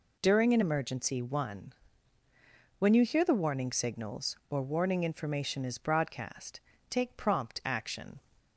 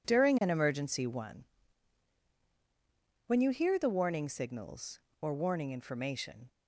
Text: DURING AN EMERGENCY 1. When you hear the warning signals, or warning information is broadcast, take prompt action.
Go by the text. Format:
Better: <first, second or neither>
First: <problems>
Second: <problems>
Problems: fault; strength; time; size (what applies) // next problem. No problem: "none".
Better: first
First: none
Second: stops before "is broadcast take prompt action"; at 6.4 s